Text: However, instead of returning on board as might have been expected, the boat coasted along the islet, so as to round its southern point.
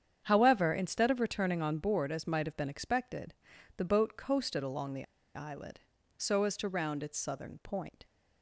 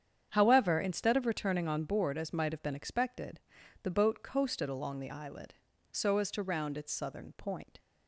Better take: second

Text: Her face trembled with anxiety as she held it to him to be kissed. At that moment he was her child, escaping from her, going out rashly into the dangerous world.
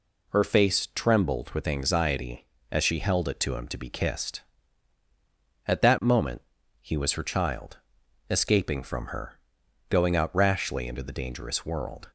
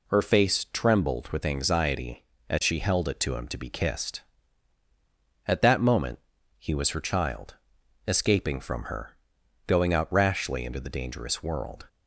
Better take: neither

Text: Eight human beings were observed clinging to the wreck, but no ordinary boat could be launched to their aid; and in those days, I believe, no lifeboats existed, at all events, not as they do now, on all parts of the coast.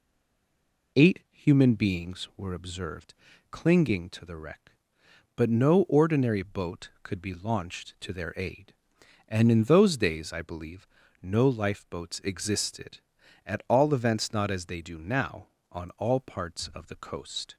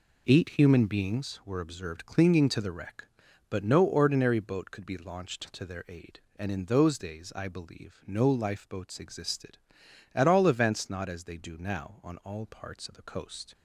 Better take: second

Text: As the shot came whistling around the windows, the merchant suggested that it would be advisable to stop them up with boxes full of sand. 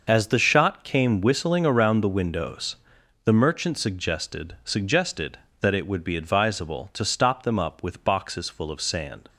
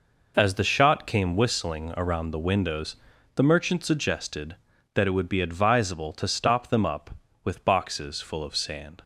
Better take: second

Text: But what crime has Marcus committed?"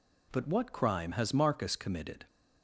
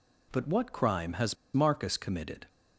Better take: first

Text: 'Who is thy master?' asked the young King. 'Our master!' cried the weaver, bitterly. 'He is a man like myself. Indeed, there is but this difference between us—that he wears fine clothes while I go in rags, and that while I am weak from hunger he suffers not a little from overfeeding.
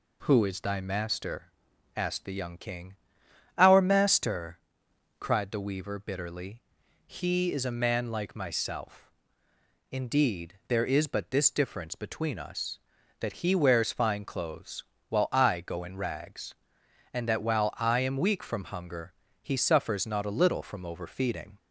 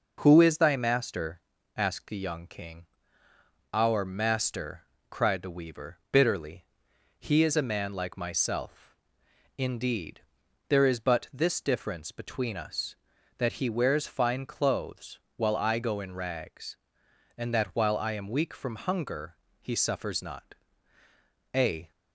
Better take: first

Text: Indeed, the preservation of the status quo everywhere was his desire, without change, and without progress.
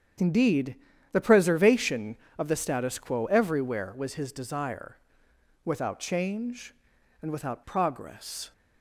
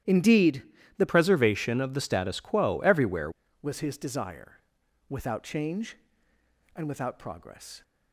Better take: first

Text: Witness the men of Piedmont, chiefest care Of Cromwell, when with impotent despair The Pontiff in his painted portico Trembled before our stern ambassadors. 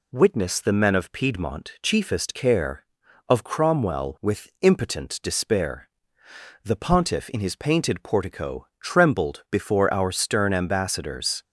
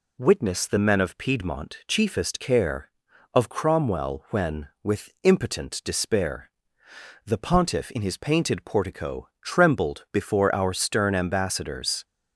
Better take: second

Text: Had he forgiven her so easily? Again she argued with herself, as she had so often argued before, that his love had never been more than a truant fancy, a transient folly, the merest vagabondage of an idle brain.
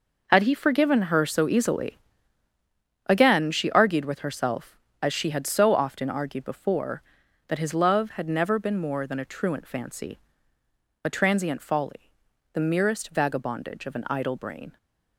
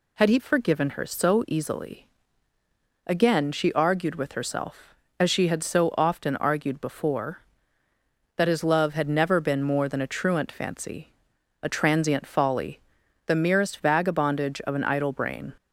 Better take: second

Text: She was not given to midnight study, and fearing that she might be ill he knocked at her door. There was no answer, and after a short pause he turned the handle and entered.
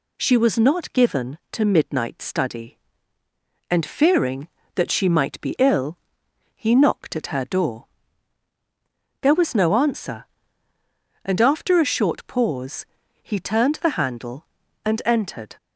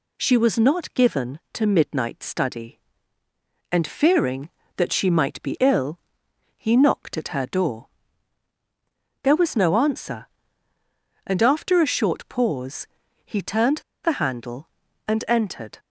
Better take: first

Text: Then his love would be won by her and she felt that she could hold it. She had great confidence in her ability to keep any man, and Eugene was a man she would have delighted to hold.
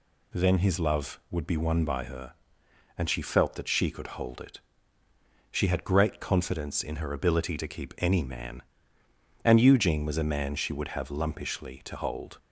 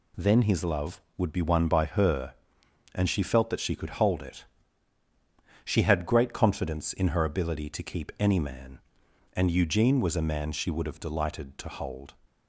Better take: second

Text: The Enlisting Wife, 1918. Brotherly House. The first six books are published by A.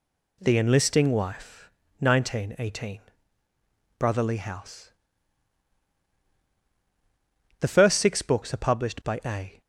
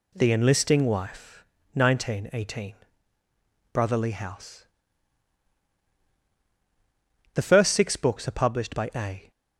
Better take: neither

